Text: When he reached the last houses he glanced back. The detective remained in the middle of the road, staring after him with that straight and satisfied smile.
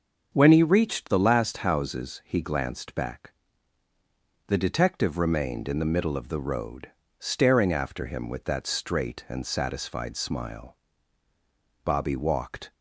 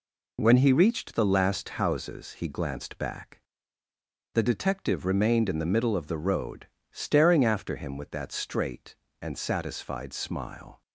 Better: second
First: starts louder than the rest; until 1.3 s; 6.5 dB // goes on to say "Bobby walked"; noticeable; from 11.8 s on; 0.88 s long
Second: none

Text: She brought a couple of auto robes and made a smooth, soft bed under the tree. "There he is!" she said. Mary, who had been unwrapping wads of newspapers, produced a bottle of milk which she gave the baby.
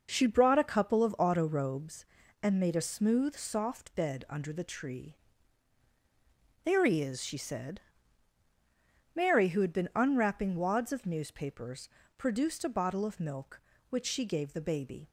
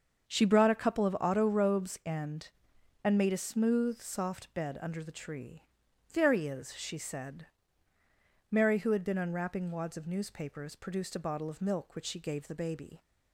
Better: first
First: none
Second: starts louder than the rest; until 1.3 s; 7 dB // says "and" twice; at 3.0 s

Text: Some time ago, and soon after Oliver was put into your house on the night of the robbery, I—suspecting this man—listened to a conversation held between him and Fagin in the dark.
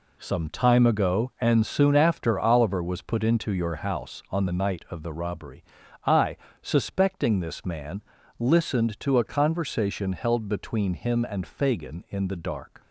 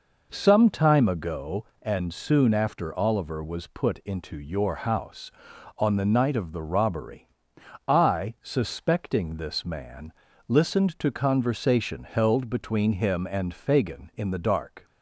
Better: first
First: none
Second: skips "a"; at 11.0 s

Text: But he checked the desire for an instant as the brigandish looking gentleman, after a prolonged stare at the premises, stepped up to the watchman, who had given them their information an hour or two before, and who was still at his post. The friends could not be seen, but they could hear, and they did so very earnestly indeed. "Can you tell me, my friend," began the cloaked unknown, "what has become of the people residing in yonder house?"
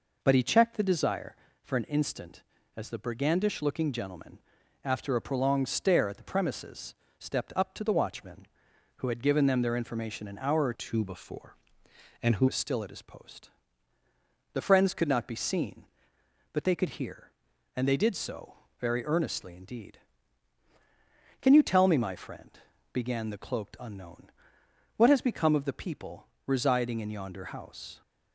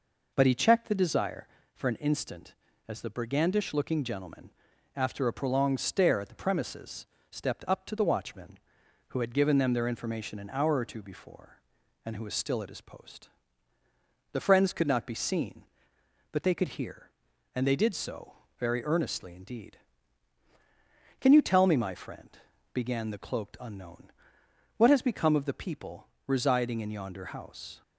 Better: second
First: changes voice from "two" to "who"; from 10.7 to 12.4 s; 1.7 s long // pauses between "so" and "very"; slight; at 18.5 s; 0.24 s long // pauses between "people" and "residing"; slight; at 26.2 s; 0.18 s long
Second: pauses between "so" and "very"; slight; at 18.3 s; 0.24 s long // pauses between "people" and "residing"; slight; at 26.0 s; 0.18 s long

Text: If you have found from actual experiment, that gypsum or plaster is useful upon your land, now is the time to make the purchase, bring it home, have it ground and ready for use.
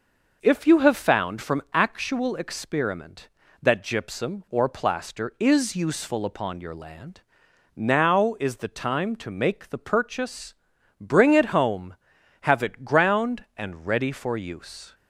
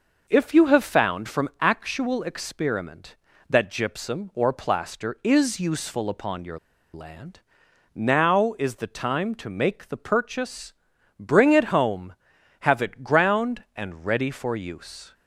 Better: first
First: none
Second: pauses between "your" and "land"; slight; at 6.5 s; 0.35 s long

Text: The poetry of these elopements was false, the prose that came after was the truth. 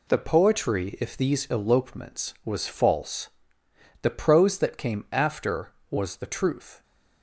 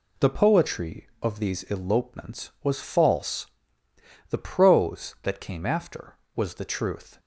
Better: second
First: says "if" for "of"; at 1.0 s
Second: none

